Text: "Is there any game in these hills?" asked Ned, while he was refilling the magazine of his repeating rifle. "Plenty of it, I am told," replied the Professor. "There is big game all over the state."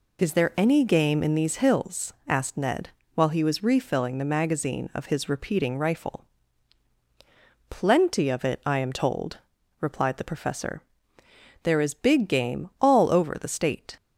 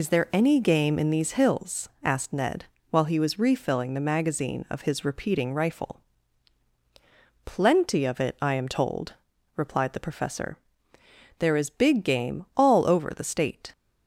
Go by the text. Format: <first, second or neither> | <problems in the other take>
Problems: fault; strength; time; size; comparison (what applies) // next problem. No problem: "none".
first | loses the start of "Is"; at 0.0 s; 55 ms